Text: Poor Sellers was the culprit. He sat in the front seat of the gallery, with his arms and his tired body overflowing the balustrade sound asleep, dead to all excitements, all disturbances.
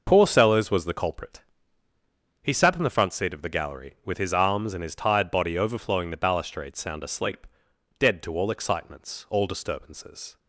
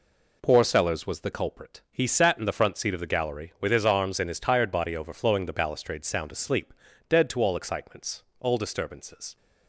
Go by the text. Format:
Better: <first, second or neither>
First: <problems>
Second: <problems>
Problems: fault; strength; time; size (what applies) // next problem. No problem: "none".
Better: neither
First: none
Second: none